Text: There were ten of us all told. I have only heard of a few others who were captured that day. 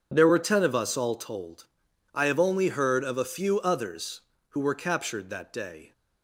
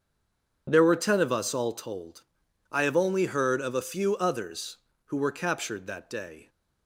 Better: first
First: none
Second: stays silent before the first word; slight; until 0.6 s; 0.6 s long // starts louder than the rest; strong; until 1.7 s; 7.5 dB

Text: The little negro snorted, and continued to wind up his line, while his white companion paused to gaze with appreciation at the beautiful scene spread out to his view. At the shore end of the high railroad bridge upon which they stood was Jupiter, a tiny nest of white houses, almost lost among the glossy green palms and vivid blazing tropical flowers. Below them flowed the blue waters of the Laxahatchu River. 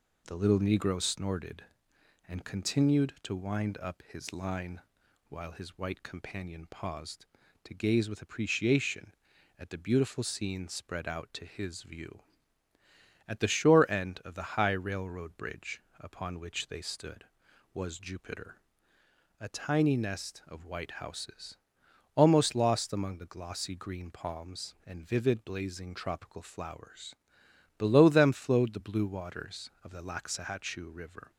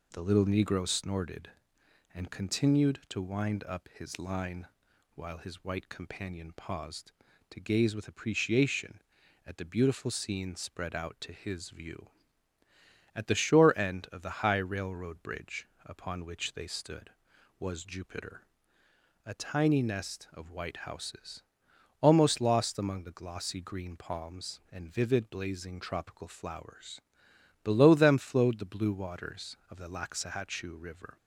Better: neither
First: pauses between "bridge" and "upon"; slight; at 15.8 s; 0.18 s long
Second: pauses between "bridge" and "upon"; slight; at 15.6 s; 0.18 s long

